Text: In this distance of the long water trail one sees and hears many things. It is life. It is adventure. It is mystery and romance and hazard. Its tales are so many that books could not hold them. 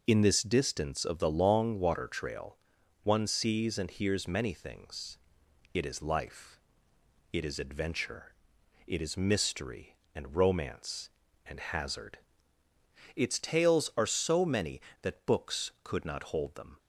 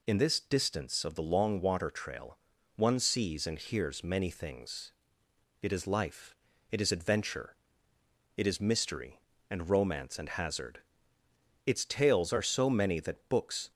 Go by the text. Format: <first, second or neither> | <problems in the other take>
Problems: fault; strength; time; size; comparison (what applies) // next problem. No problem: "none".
first | pauses between "trail" and "one"; at 2.3 s; 0.38 s long; also in the first // stops before "could not hold them"; at 13.7 s